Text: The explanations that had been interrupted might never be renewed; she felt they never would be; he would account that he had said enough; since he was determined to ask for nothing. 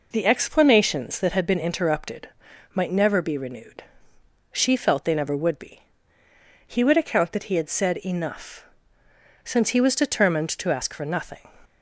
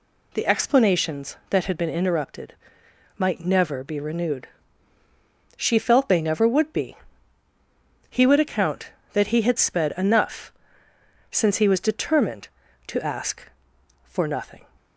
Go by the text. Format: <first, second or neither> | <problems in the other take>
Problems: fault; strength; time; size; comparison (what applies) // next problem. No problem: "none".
first | pauses between "interrupted" and "might"; noticeable; at 2.5 s; 0.64 s long; noticeable in the first // says "sped" for "said"; at 9.5 s